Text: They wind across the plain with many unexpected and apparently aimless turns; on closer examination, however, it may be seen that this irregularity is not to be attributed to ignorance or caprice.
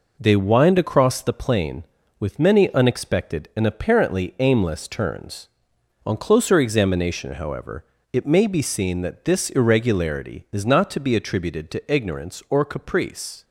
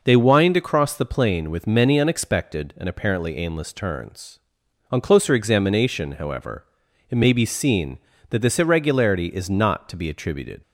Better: first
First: none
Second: stops before "to ignorance or caprice"; at 10.6 s

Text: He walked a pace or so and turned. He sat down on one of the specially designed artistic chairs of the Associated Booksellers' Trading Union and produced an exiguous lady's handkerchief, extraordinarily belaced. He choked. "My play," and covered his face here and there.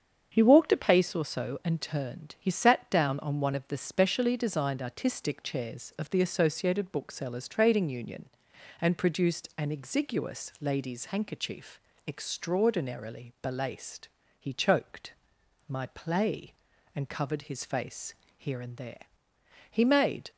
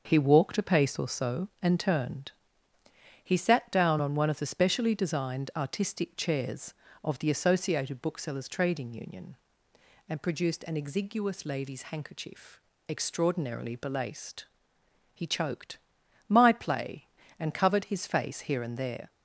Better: second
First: starts louder than the rest; strong; until 1.3 s; 7.5 dB // pauses between "face" and "here"; slight; at 18.1 s; 0.24 s long // goes on to say "He made"; from 19.7 s on; 0.60 s long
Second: starts louder than the rest; until 1.0 s; 6.5 dB

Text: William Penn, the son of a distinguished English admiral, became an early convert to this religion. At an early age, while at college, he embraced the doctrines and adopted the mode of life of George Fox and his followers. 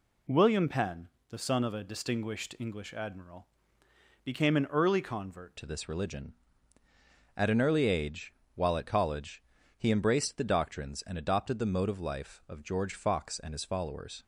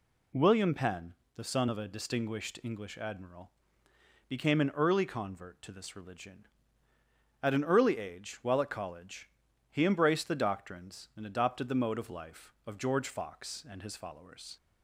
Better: second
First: changes voice at "to"; from 5.5 s on; 8.7 s long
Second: none

